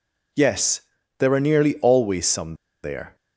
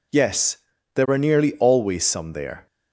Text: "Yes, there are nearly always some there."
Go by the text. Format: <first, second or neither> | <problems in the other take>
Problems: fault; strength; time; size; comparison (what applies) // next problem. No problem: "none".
second | pauses between "some" and "there"; slight; at 2.5 s; 0.29 s long